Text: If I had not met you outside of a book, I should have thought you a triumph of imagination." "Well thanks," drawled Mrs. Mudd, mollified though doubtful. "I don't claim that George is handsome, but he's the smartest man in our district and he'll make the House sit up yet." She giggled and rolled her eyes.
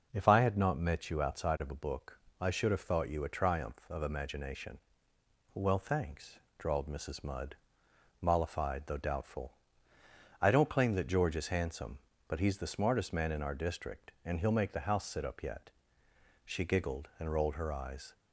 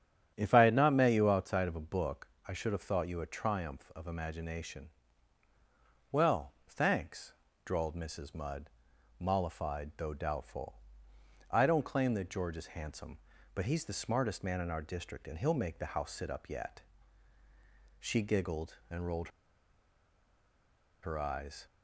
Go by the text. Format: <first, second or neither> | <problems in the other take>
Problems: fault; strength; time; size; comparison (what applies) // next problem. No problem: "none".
first | starts louder than the rest; strong; until 1.3 s; 9.5 dB // pauses between "rolled" and "her"; strong; at 19.2 s; 1.7 s long